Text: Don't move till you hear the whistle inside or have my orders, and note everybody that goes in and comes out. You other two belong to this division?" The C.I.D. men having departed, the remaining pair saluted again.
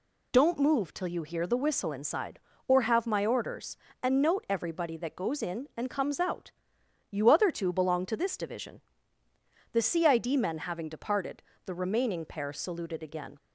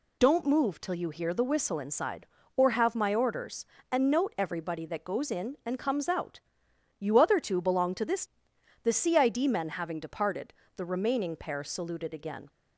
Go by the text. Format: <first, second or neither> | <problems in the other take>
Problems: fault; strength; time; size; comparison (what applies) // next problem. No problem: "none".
first | skips "division"; at 8.5 s